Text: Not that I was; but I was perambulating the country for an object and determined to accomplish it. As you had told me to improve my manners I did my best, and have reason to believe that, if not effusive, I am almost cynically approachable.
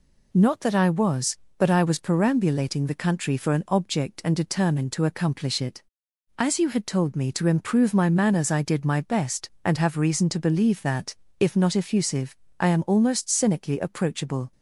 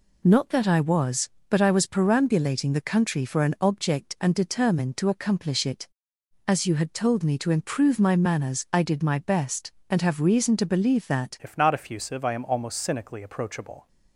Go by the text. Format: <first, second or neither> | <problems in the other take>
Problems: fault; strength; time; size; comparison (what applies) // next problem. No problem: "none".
first | changes voice at "if"; from 11.4 s on; 2.4 s long